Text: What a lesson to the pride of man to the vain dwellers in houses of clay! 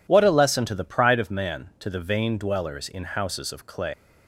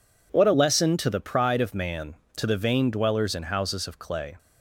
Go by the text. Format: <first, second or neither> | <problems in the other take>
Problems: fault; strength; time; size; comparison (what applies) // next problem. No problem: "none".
second | leaves "clay" unfinished; at 3.9 s; 110 ms